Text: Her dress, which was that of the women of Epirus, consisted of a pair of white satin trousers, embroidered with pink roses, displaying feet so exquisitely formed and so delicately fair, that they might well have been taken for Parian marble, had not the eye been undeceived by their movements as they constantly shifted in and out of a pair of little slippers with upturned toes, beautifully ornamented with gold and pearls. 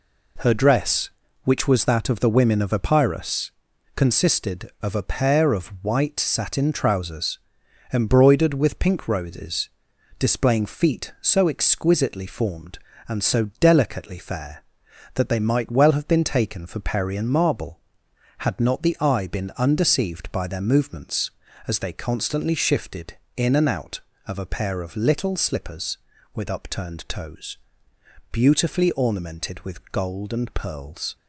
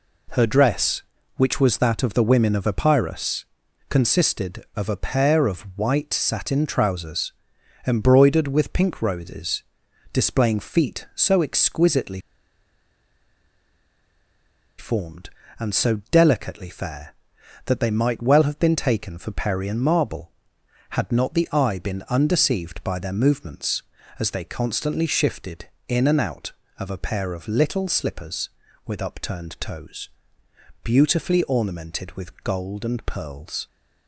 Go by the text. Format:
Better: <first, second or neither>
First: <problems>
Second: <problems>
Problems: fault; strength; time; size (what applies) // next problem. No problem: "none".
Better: first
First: none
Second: pauses between "exquisitely" and "formed"; strong; at 12.1 s; 2.5 s long